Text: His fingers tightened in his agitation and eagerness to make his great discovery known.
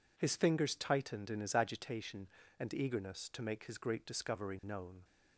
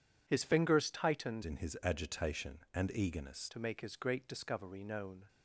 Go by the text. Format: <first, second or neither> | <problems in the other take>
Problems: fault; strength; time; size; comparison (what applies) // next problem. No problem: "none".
first | changes voice from "in" to "eagerness"; from 1.4 to 3.5 s; 2.1 s long